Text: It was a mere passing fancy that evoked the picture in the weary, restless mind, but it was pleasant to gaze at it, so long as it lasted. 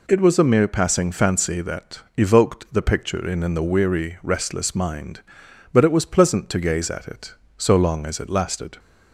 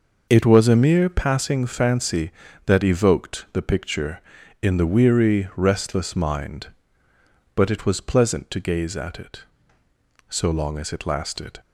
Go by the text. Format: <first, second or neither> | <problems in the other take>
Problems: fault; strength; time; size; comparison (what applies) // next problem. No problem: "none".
second | pauses between "that" and "evoked"; slight; at 2.0 s; 0.16 s long // says "in" twice; at 3.4 s